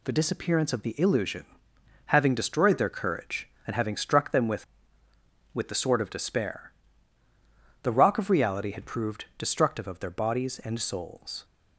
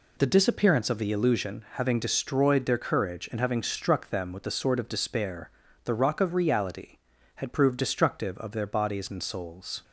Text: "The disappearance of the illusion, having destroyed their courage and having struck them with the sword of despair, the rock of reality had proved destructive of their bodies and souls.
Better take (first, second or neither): second